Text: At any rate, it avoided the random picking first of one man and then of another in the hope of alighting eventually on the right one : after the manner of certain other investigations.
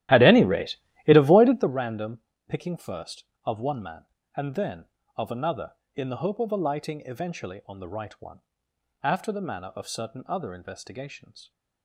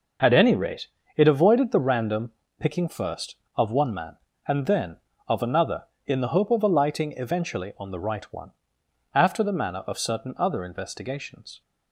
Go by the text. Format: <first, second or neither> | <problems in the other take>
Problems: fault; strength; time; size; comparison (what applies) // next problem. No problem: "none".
second | starts louder than the rest; strong; until 1.7 s; 14 dB // pauses between "random" and "picking"; slight; at 2.2 s; 0.26 s long; slight in the second